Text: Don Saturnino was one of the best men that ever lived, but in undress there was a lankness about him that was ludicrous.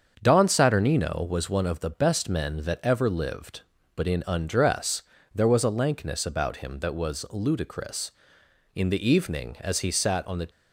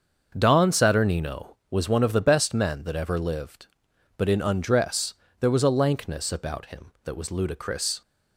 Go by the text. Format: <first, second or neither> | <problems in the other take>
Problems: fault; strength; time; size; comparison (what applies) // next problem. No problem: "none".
second | starts louder than the rest; strong; until 1.2 s; 7 dB; also in the second // pauses between "undress" and "there"; slight; at 5.0 s; 0.32 s long; slight in the second // goes on to say "In the evening as he sat on the"; strong; from 8.7 s on; 1.7 s long